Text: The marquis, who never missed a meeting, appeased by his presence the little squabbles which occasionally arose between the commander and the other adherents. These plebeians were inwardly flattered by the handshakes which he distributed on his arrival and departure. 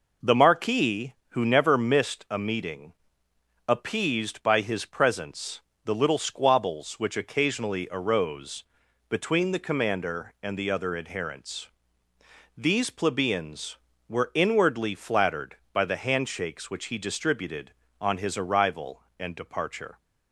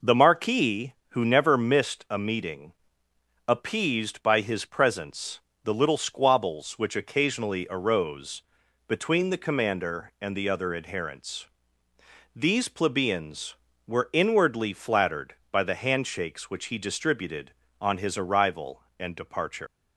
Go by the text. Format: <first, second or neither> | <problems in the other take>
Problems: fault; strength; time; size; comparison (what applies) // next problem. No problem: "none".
first | pauses between "presence" and "the"; slight; at 5.3 s; 0.24 s long; slight in the first // pauses between "arose" and "between"; at 8.4 s; 0.44 s long; also in the first // leaves "departure" unfinished; at 19.6 s; 120 ms